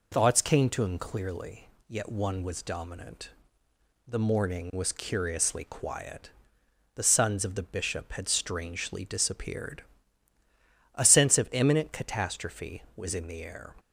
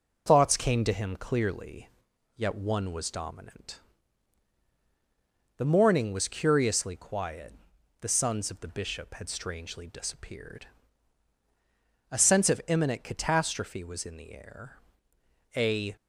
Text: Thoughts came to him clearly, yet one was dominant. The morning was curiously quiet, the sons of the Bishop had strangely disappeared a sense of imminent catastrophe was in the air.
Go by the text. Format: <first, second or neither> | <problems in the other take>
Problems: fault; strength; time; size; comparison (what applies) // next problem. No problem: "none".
first | pauses between "disappeared" and "a"; strong; at 10.6 s; 1.4 s long; also in the first // goes on to say "A"; slight; from 15.5 s on; 0.40 s long